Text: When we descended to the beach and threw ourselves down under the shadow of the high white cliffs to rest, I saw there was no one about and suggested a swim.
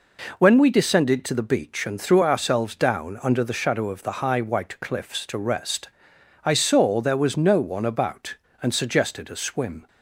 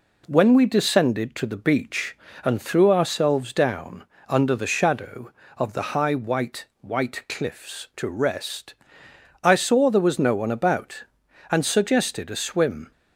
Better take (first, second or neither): first